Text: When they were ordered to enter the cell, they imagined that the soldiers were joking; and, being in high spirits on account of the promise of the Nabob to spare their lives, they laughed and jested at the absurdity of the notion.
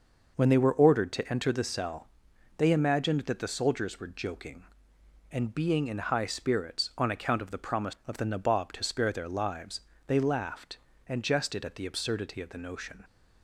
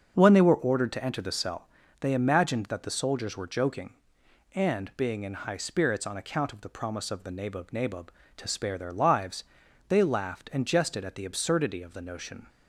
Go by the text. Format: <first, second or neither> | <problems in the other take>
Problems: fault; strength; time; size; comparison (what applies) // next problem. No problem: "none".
first | starts louder than the rest; until 1.1 s; 7 dB // says "Nabob" twice; at 7.7 s